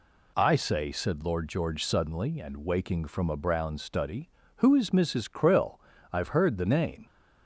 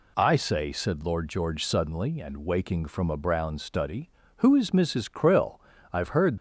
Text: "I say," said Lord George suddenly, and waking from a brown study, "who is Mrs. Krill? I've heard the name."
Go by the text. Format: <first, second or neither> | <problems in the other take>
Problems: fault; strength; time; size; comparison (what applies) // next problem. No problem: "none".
first | stops before "the name"; at 6.3 s